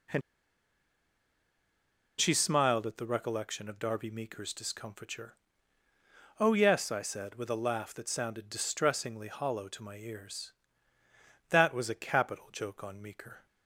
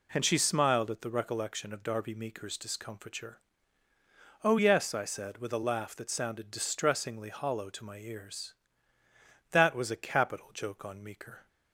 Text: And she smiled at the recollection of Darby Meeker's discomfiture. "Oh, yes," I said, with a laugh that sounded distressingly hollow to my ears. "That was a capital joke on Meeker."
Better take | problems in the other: second | pauses between "And" and "she"; strong; at 0.2 s; 1.9 s long

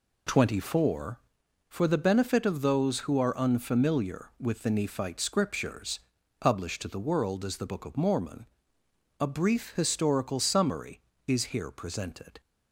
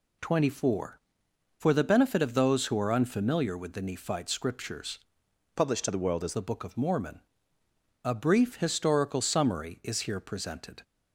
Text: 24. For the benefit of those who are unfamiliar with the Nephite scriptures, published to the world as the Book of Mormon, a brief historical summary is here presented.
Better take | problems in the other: first | changes voice from "published" to "as"; from 5.5 to 6.3 s; 0.8 s long

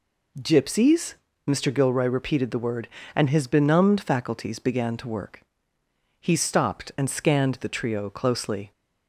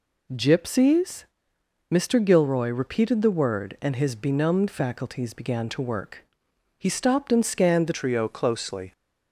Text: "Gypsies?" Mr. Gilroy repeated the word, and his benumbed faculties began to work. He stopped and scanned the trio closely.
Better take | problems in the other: first | changes voice at "trio"; from 7.9 s on; 1.0 s long

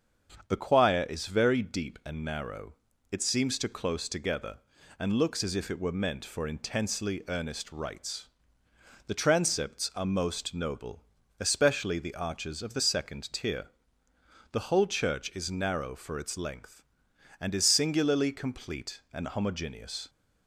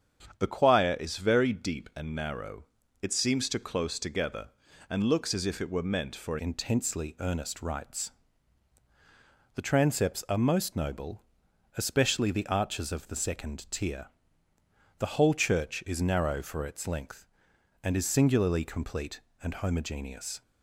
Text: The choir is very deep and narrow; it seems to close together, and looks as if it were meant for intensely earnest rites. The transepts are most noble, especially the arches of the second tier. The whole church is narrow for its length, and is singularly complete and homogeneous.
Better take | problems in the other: first | starts louder than the rest; strong; until 1.4 s; 8 dB; strong in the first // changes voice at "intensely"; from 6.3 s on; 14.1 s long

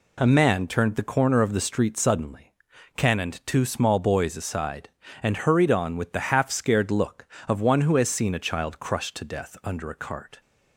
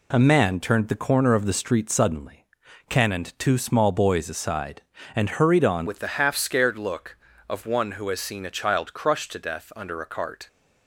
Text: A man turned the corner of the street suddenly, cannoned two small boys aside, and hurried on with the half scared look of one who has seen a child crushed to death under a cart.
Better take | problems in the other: first | changes voice at "with"; from 5.8 s on; 4.6 s long

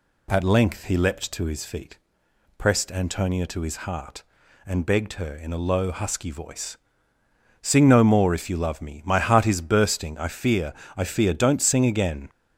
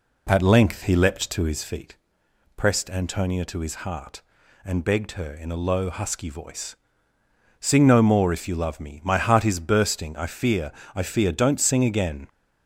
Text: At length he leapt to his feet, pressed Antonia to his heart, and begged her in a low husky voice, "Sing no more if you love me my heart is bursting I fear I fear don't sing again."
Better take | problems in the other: first | starts louder than the rest; slight; until 1.9 s; 3 dB // pauses between "fear" and "I"; slight; at 10.6 s; 0.24 s long; slight in the first

